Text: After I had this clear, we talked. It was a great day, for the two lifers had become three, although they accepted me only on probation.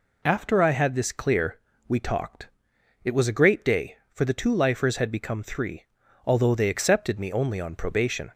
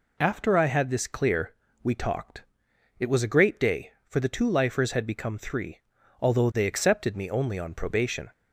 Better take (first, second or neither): neither